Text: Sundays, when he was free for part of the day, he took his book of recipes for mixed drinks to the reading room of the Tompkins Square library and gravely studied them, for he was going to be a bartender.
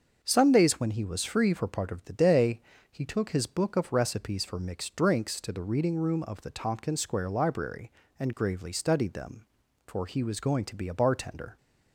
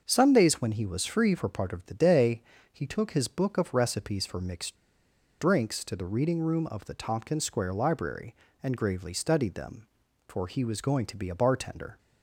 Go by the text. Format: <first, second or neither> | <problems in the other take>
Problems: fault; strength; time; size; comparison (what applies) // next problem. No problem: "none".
first | starts louder than the rest; until 1.0 s; 6.5 dB; also in the first // pauses between "mixed" and "drinks"; noticeable; at 4.7 s; 0.63 s long